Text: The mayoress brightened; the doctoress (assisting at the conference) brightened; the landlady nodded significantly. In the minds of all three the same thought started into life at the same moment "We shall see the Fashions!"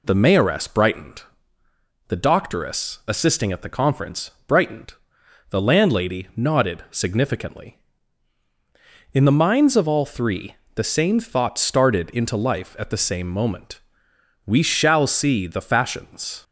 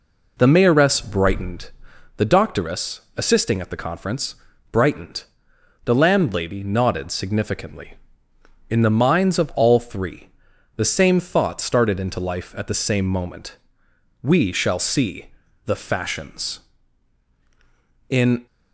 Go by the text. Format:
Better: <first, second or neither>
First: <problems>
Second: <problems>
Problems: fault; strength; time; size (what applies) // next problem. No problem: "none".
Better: first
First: pauses between "three" and "the"; slight; at 10.5 s; 0.18 s long // pauses between "moment" and "We"; noticeable; at 13.7 s; 0.66 s long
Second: pauses between "three" and "the"; noticeable; at 10.2 s; 0.46 s long // pauses between "moment" and "We"; noticeable; at 13.5 s; 0.66 s long // pauses between "see" and "the"; slight; at 15.3 s; 0.34 s long // goes on to say "In"; slight; from 18.0 s on; 0.38 s long